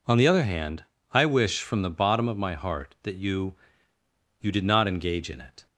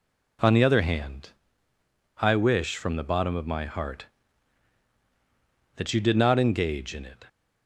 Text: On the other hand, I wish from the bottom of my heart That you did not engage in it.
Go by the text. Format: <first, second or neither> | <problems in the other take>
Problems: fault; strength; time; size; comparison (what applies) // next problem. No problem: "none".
second | says "you" twice; at 4.4 s